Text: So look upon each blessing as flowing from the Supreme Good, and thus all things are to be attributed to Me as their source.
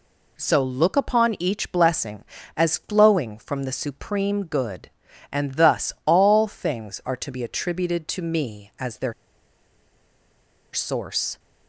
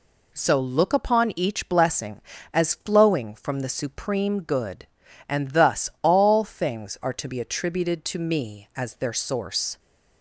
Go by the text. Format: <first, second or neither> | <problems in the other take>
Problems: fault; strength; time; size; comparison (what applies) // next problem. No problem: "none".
second | pauses between "their" and "source"; strong; at 9.1 s; 1.6 s long